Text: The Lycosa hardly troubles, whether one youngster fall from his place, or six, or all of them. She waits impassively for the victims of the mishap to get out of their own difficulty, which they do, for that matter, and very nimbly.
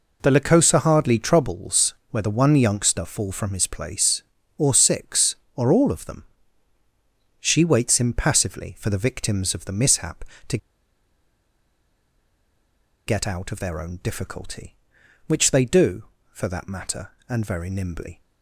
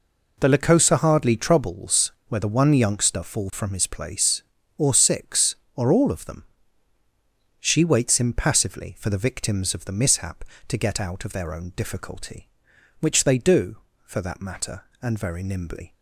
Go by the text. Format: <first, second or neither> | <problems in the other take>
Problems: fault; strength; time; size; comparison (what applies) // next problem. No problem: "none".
second | pauses between "to" and "get"; strong; at 10.5 s; 2.4 s long